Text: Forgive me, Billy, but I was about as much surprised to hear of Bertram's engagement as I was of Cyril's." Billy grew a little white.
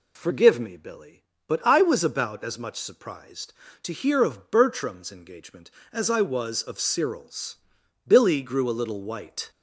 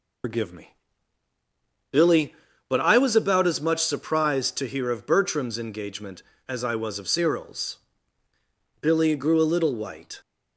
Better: first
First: none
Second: loses the start of "Forgive"; at 0.2 s; 100 ms

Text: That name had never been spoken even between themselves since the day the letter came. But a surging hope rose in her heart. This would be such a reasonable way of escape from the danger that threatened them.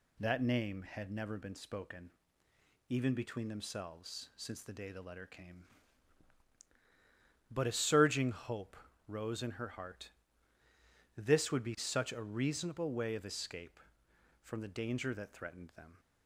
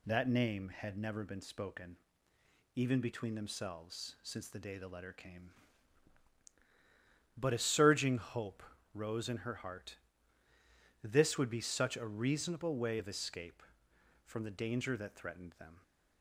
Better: neither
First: pauses between "spoken" and "even"; noticeable; at 2.0 s; 0.80 s long // pauses between "hope" and "rose"; slight; at 8.7 s; 0.30 s long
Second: pauses between "spoken" and "even"; noticeable; at 1.9 s; 0.80 s long // pauses between "hope" and "rose"; slight; at 8.6 s; 0.30 s long

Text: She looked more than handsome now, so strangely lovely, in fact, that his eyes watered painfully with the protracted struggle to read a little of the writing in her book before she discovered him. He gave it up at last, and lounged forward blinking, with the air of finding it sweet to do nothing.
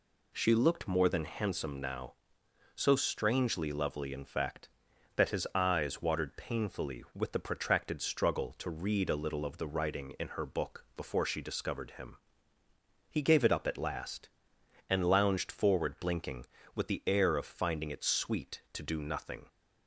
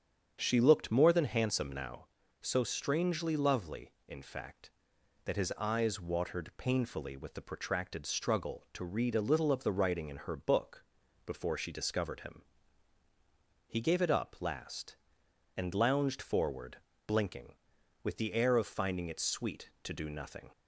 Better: first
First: none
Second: starts louder than the rest; strong; until 1.4 s; 7.5 dB // pauses between "book" and "before"; at 10.8 s; 0.40 s long // skips "at"; at 14.3 s // pauses between "forward" and "blinking"; slight; at 16.7 s; 0.28 s long

